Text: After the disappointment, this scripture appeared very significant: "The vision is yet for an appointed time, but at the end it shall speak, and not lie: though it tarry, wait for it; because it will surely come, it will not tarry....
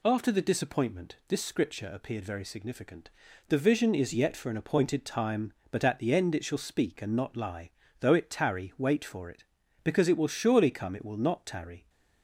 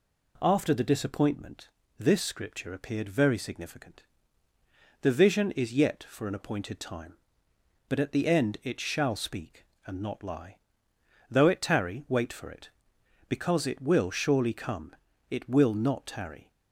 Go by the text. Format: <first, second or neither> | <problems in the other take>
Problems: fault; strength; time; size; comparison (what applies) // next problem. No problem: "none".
neither | none